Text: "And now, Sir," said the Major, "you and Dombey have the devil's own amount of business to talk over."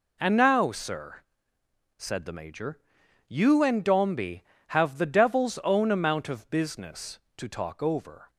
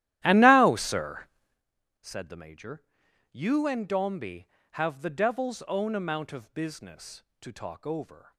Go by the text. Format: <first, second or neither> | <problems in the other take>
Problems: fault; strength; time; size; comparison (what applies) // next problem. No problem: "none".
first | starts louder than the rest; strong; until 1.6 s; 13 dB